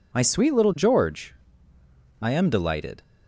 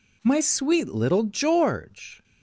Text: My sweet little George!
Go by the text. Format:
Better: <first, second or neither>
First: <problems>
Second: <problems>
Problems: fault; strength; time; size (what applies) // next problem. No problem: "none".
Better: second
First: goes on to say "I am delighted"; noticeable; from 2.1 s on; 0.82 s long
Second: none